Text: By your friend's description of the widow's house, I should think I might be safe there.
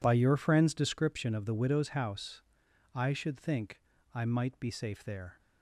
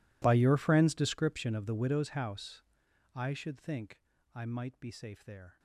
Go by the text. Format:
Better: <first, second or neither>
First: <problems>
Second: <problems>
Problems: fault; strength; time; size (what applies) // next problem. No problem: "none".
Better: first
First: pauses between "think" and "I"; slight; at 3.7 s; 0.34 s long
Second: gets quieter; strong; throughout; 23.5 dB // pauses between "think" and "I"; slight; at 3.9 s; 0.34 s long